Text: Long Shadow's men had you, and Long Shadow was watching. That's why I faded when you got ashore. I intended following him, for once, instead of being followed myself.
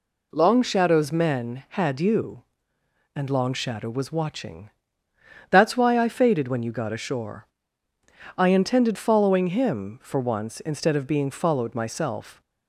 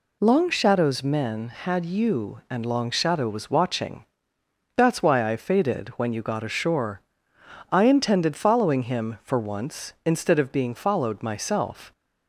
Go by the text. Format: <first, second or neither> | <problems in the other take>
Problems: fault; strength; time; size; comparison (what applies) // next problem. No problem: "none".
neither | none